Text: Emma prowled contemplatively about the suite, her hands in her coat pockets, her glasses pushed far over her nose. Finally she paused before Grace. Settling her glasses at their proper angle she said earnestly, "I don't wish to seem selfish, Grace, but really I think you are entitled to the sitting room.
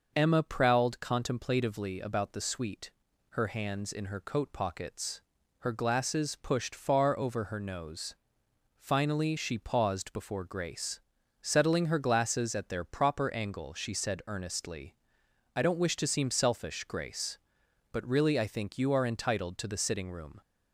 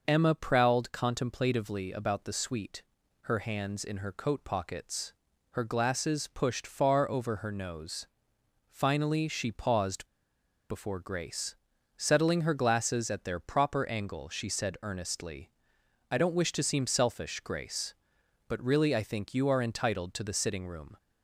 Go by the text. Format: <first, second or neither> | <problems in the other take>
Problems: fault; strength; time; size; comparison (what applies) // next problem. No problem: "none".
first | pauses between "paused" and "before"; noticeable; at 10.0 s; 0.64 s long